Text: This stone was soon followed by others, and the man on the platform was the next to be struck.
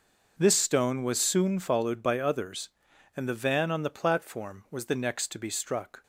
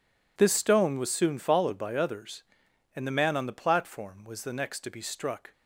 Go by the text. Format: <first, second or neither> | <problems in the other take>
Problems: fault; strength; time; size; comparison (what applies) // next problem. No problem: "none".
second | says "van" for "man"; at 3.3 s